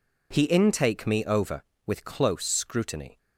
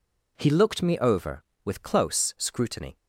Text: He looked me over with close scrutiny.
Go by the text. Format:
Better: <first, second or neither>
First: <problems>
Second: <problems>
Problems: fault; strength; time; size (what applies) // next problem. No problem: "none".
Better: second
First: says "intake" for "looked"; at 0.4 s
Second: none